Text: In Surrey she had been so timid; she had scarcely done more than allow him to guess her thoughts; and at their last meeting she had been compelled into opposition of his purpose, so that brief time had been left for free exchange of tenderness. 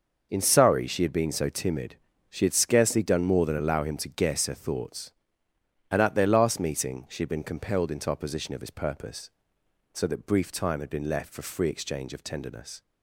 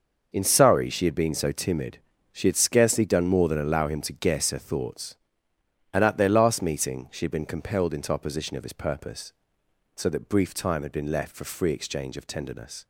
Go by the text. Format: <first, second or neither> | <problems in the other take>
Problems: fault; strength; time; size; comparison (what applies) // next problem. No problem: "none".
neither | none